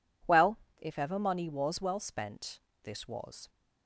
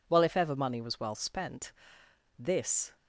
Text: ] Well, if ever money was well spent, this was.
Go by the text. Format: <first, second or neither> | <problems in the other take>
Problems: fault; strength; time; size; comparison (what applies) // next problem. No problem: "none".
first | stops before "was"; at 2.9 s